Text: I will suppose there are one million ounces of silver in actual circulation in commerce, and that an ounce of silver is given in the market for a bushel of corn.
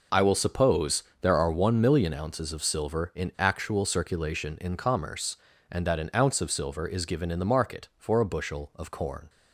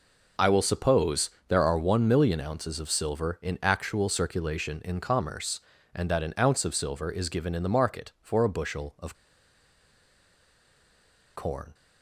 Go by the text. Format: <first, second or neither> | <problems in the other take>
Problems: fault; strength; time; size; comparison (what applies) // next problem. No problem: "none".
first | pauses between "suppose" and "there"; slight; at 1.3 s; 0.16 s long; slight in the first // pauses between "of" and "corn"; strong; at 9.1 s; 2.2 s long